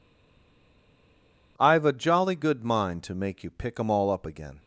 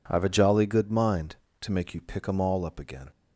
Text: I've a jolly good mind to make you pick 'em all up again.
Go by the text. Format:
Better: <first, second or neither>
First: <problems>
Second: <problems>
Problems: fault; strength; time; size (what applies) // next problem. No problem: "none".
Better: second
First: stays silent before the first word; noticeable; until 1.5 s; 1.5 s long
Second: none